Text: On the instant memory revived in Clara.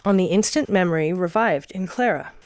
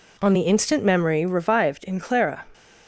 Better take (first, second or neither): neither